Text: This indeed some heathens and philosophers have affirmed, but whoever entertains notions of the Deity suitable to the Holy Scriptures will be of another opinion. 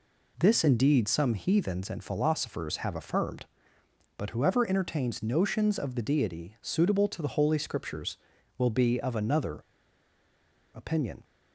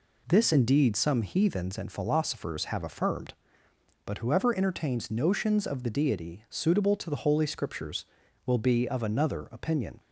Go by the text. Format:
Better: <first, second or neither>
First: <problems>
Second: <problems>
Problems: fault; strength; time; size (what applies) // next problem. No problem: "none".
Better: second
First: pauses between "another" and "opinion"; at 9.6 s; 1.1 s long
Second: none